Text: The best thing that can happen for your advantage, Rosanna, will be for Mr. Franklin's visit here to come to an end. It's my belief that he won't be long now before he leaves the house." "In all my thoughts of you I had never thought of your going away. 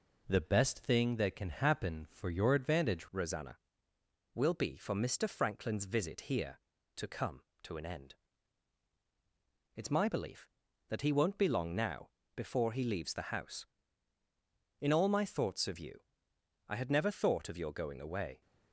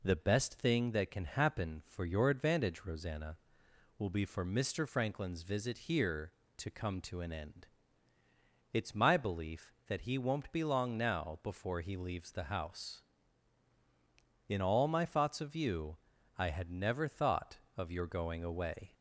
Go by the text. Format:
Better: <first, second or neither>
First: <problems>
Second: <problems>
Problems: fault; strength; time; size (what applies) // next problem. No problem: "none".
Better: second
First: changes voice at "Rosanna"; from 3.1 s on; 15.3 s long // pauses between "now" and "before"; slight; at 12.1 s; 0.26 s long // pauses between "you" and "I"; noticeable; at 16.0 s; 0.64 s long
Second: pauses between "you" and "I"; at 15.9 s; 0.40 s long